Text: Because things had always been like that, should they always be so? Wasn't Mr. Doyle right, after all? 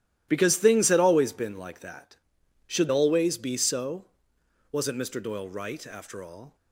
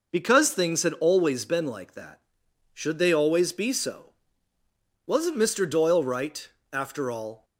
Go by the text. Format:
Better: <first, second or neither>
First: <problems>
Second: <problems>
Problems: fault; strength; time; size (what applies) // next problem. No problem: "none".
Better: second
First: starts louder than the rest; strong; until 1.3 s; 13.5 dB // skips "they"; at 2.8 s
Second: none